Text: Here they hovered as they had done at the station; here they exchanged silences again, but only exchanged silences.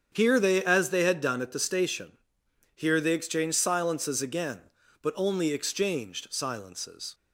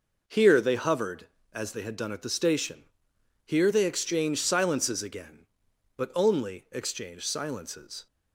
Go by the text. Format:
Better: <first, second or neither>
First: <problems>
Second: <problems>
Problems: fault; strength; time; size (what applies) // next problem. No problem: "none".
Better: second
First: starts louder than the rest; strong; until 1.1 s; 7.5 dB // skips "hovered"; at 0.6 s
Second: none